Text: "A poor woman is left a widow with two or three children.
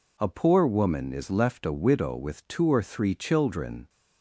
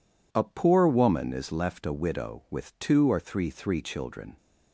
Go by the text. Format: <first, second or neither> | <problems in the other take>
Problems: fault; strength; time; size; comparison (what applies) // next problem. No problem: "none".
first | says "three" twice; at 3.5 s